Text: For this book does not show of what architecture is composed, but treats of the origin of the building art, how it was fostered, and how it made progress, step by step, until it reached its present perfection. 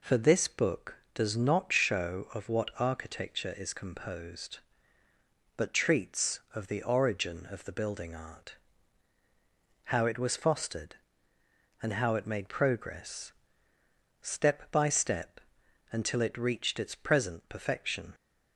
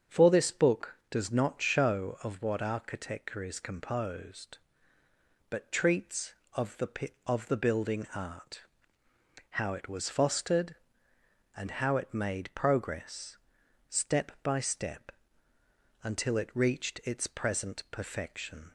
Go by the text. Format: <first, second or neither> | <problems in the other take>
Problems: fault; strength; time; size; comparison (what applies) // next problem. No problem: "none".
first | starts louder than the rest; strong; until 1.2 s; 7.5 dB // skips "origin"; at 7.2 s